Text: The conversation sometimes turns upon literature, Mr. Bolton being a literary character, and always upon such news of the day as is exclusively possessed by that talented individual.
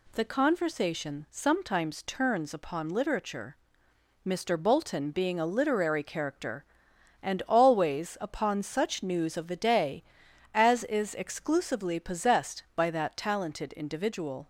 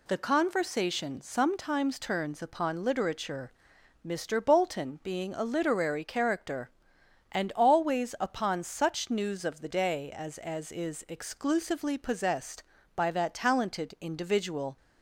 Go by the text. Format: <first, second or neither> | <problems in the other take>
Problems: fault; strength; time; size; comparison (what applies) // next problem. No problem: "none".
first | says "as" twice; at 10.3 s